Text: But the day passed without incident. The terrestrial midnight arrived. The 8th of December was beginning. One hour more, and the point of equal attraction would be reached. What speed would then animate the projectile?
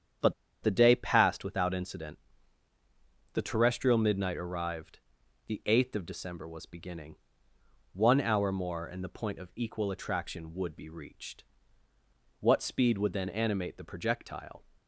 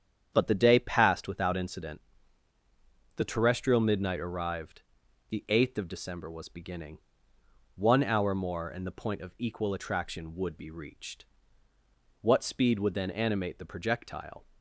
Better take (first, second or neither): second